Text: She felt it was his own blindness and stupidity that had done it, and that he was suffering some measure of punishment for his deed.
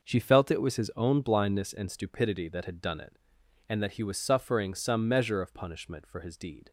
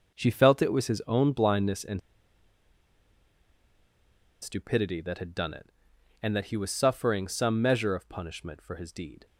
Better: first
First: none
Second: pauses between "and" and "stupidity"; strong; at 2.0 s; 2.4 s long

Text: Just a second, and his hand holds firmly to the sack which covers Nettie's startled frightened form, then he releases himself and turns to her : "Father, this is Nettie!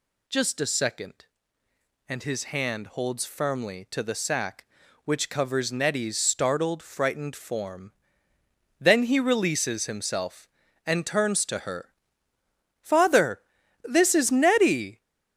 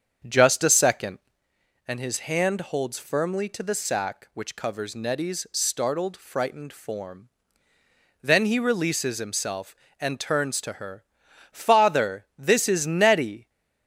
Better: first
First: none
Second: starts louder than the rest; strong; until 1.6 s; 7.5 dB

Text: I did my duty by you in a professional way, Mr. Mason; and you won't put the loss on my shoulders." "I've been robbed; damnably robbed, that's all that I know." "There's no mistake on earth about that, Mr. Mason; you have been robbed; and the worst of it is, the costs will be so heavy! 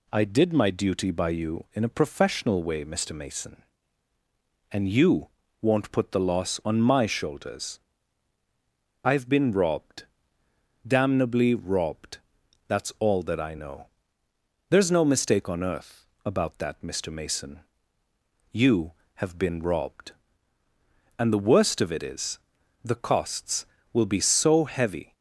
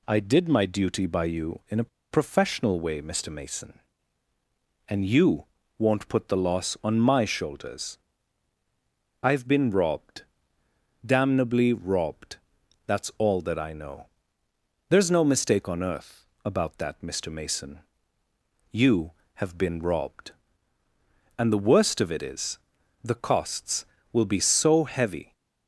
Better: first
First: pauses between "you" and "won't"; slight; at 5.2 s; 0.32 s long // pauses between "earth" and "about"; slight; at 16.0 s; 0.18 s long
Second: pauses between "a" and "professional"; slight; at 1.8 s; 0.22 s long // pauses between "you" and "won't"; slight; at 5.4 s; 0.32 s long // pauses between "earth" and "about"; slight; at 16.2 s; 0.18 s long

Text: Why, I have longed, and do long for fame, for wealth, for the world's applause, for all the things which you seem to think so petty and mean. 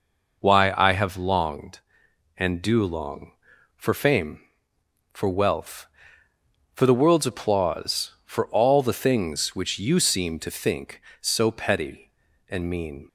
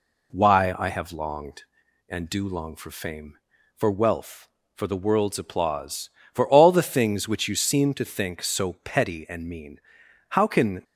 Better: first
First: none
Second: goes on to say "How can"; from 10.2 s on; 0.54 s long

